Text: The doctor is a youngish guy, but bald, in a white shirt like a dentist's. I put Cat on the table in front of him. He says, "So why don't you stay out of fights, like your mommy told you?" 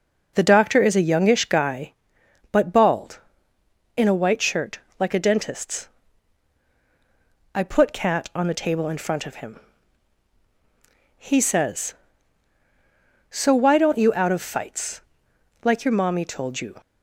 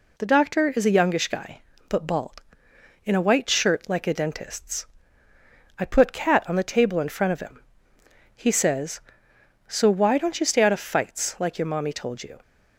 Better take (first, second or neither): second